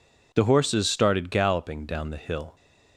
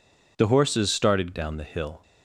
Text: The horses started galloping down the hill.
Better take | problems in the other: first | skips "galloping"; at 1.3 s

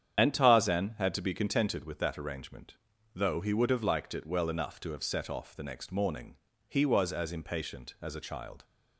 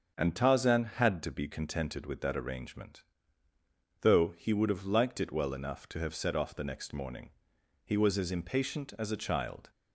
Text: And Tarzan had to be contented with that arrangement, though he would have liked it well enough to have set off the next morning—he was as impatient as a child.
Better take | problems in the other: second | loses the start of "And"; at 0.1 s; 60 ms // starts louder than the rest; strong; until 1.2 s; 8.5 dB; also in the second

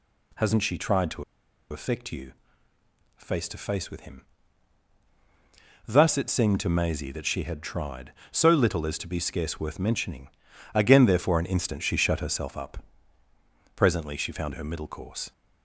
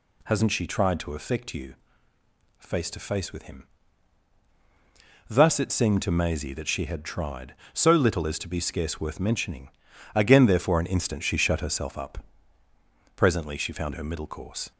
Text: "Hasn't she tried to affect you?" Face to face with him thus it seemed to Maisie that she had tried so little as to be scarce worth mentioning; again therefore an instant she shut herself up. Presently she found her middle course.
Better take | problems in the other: second | pauses between "to" and "affect"; noticeable; at 1.2 s; 0.47 s long // pauses between "him" and "thus"; strong; at 4.2 s; 1.6 s long; strong in the second

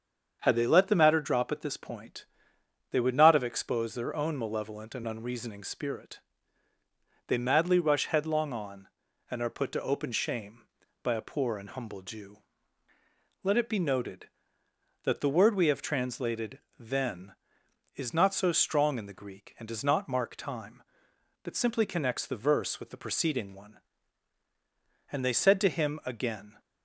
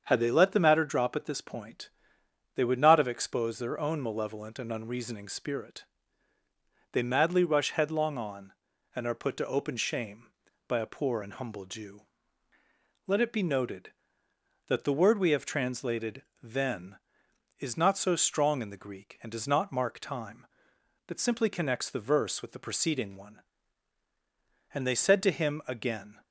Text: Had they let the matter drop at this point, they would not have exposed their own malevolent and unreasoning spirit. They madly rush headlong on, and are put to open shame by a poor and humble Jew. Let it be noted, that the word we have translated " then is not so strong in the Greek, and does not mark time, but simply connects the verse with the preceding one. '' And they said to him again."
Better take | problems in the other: neither | starts louder than the rest; strong; the same in both

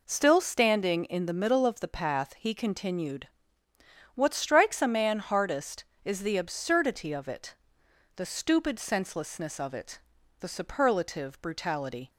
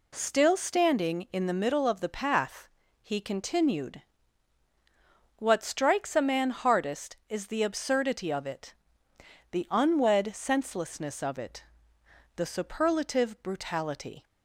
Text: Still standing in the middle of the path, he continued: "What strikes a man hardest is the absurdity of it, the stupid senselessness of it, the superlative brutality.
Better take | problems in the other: first | says "unwed" for "stupid"; at 9.7 s

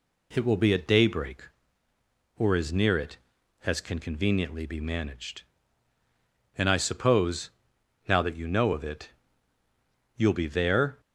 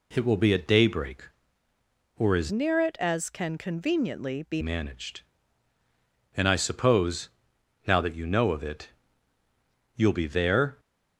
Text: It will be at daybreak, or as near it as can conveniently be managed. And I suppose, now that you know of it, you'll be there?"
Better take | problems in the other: first | changes voice from "near" to "be"; from 2.5 to 4.6 s; 2.1 s long

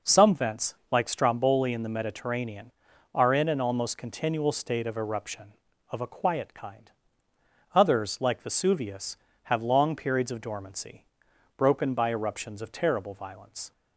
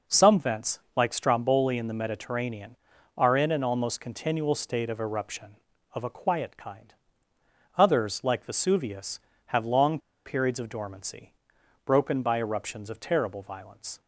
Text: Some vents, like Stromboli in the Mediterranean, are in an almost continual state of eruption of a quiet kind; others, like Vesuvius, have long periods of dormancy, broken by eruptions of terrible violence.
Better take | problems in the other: first | pauses between "long" and "periods"; slight; at 9.9 s; 0.27 s long

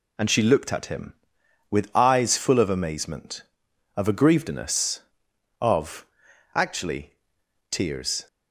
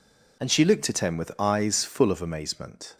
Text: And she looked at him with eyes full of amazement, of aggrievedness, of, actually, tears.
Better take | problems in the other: first | stops before "of aggrievedness of actually tears"; at 2.9 s

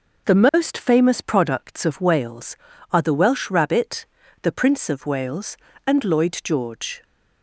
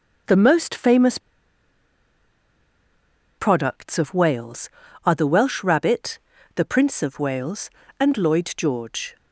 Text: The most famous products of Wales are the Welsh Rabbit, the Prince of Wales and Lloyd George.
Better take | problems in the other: first | pauses between "famous" and "products"; strong; at 1.1 s; 2.1 s long

